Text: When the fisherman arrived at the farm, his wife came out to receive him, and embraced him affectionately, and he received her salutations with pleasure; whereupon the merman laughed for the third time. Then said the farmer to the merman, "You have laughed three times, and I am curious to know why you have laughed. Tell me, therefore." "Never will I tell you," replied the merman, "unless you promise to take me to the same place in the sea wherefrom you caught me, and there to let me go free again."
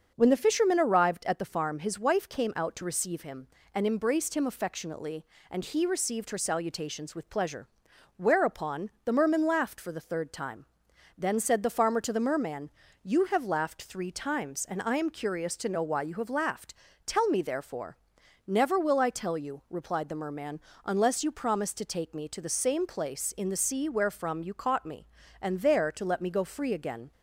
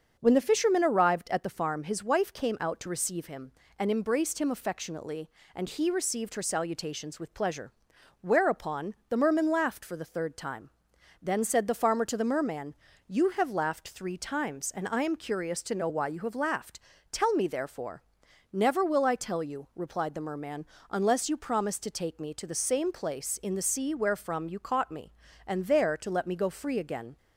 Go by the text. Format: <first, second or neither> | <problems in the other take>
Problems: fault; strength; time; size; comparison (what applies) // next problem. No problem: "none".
neither | starts louder than the rest; the same in both